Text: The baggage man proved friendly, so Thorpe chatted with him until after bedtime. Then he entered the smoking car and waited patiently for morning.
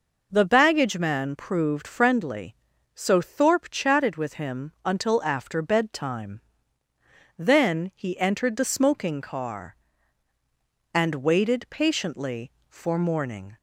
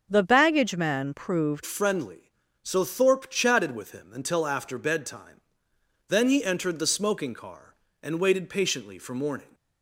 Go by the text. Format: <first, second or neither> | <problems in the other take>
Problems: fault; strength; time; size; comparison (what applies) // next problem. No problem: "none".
first | starts louder than the rest; until 1.1 s; 6.5 dB // changes voice at "friendly"; from 1.6 s on; 7.8 s long